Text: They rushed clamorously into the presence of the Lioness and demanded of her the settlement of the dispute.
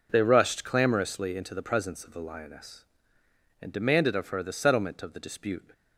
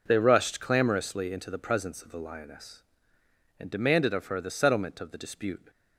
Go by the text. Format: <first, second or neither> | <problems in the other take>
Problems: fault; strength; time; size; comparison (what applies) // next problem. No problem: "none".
neither | none